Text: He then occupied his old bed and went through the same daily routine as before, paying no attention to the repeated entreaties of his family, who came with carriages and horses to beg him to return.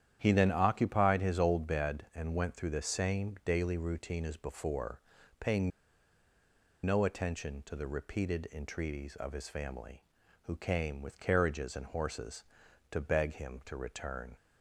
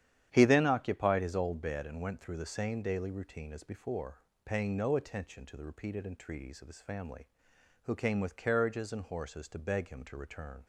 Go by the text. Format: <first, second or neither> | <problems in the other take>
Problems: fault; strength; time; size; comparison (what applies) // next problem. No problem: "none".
second | starts louder than the rest; strong; until 1.2 s; 10 dB; strong in the second // pauses between "paying" and "no"; at 5.7 s; 1.1 s long